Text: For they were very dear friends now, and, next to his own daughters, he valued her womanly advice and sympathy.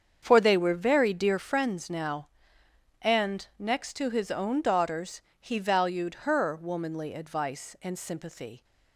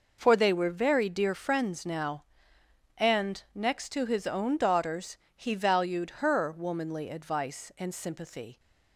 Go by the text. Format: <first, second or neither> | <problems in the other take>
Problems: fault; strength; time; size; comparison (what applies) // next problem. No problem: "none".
second | starts louder than the rest; strong; until 1.6 s; 7 dB